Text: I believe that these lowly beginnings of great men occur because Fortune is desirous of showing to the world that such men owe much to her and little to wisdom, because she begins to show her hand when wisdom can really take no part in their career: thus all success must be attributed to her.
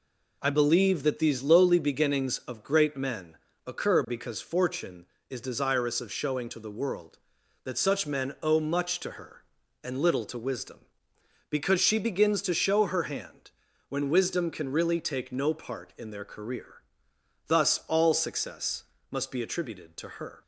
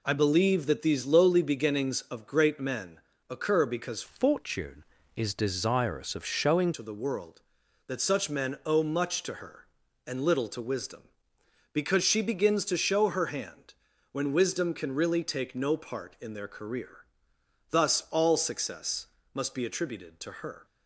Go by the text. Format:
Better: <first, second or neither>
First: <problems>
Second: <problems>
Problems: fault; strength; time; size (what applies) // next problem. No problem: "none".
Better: first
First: pauses between "men" and "occur"; slight; at 3.3 s; 0.30 s long // pauses between "hand" and "when"; slight; at 13.5 s; 0.36 s long // pauses between "success" and "must"; slight; at 18.8 s; 0.30 s long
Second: pauses between "men" and "occur"; slight; at 2.9 s; 0.30 s long // changes voice from "Fortune" to "showing"; from 4.0 to 6.7 s; 2.7 s long // pauses between "hand" and "when"; slight; at 13.7 s; 0.36 s long // pauses between "success" and "must"; slight; at 19.0 s; 0.30 s long